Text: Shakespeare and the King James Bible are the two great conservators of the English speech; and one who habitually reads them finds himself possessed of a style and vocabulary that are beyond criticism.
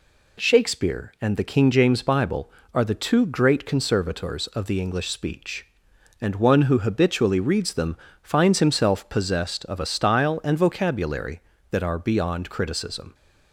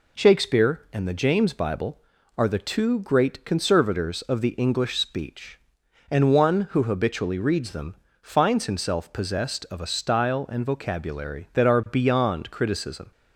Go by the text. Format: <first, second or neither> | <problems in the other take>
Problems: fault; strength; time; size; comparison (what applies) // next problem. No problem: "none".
first | skips "King"; at 1.1 s // pauses between "them" and "finds"; slight; at 7.9 s; 0.24 s long; slight in the first